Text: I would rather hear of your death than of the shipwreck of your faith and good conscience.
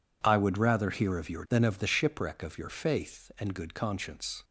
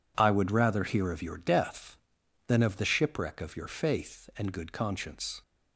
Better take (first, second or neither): second